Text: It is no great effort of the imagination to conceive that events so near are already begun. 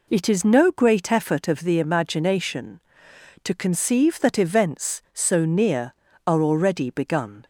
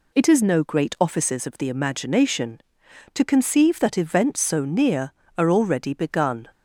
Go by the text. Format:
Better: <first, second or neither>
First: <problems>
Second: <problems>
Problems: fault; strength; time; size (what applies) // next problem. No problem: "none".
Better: first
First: none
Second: says "offices" for "effort"; at 1.0 s